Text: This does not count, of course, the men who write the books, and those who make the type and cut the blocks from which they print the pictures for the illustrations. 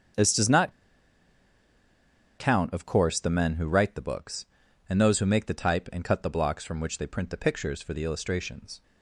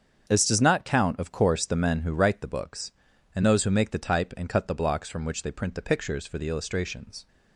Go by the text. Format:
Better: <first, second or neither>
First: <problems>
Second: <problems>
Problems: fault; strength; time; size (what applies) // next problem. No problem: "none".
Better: second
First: starts louder than the rest; strong; until 2.8 s; 7 dB // pauses between "not" and "count"; strong; at 0.7 s; 1.6 s long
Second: starts louder than the rest; until 1.3 s; 7 dB